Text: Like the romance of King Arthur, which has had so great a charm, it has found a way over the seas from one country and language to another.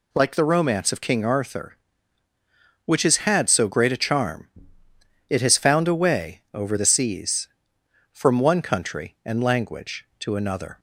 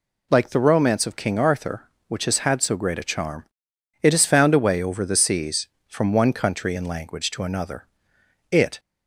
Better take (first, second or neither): first